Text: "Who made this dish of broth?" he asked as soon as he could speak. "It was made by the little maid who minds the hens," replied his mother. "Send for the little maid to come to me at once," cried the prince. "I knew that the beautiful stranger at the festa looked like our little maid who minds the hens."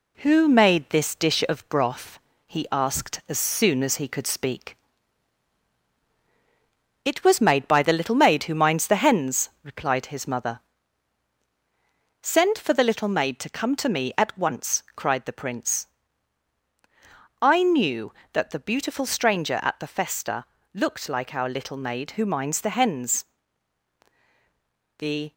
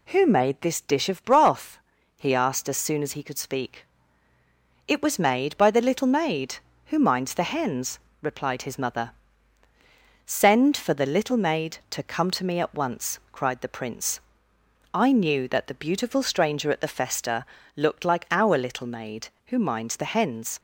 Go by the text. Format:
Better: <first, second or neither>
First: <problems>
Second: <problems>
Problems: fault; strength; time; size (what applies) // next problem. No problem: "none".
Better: second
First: pauses between "festa" and "looked"; slight; at 20.4 s; 0.30 s long // goes on to say "The"; slight; from 24.9 s on; 0.34 s long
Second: pauses between "festa" and "looked"; slight; at 17.4 s; 0.30 s long